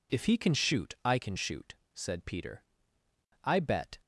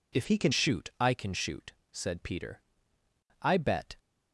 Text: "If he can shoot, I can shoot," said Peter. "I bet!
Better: first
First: none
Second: changes voice from "he" to "can"; from 0.2 to 0.5 s; 0.3 s long

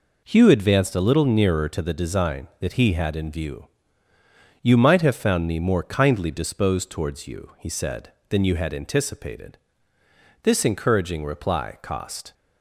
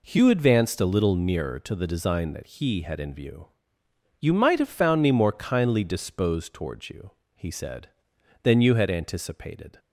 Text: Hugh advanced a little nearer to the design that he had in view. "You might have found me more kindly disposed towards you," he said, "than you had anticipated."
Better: second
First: goes on to say "This encouraging reply cost"; strong; from 10.4 s on; 1.9 s long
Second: none

